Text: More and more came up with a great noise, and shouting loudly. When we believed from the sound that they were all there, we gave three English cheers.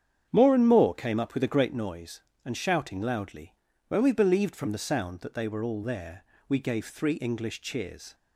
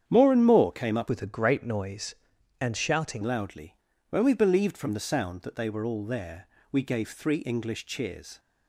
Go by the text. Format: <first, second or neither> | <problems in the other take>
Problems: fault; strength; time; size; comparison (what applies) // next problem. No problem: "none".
first | starts louder than the rest; strong; until 1.0 s; 8.5 dB; strong in the first // changes voice from "with" to "shouting"; from 1.0 to 3.2 s; 2.2 s long